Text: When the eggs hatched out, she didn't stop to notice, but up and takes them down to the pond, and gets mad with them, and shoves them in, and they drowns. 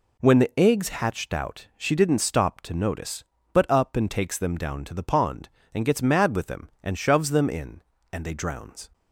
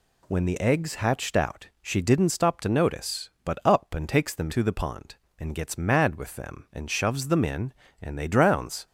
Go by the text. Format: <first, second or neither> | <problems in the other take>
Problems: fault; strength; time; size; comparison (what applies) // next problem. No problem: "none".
first | skips "down"; at 4.5 s